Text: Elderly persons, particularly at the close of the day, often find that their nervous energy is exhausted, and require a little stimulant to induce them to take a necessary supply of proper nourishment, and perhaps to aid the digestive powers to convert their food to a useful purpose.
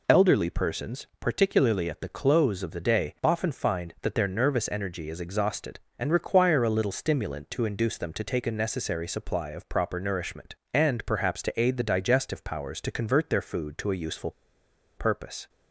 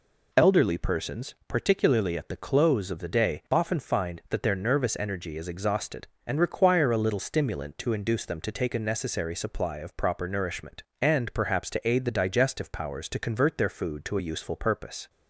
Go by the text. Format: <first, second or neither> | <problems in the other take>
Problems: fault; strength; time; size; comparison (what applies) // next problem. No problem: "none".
second | pauses between "useful" and "purpose"; noticeable; at 14.3 s; 0.67 s long